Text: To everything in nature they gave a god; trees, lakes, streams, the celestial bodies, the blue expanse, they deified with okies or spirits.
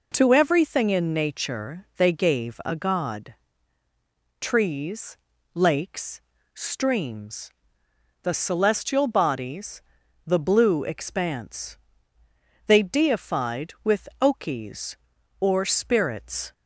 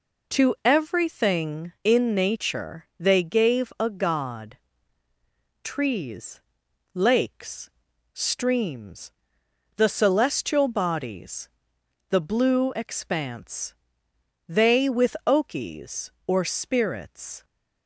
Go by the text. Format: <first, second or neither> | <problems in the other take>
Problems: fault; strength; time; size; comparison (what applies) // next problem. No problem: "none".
first | skips "deified"; at 14.8 s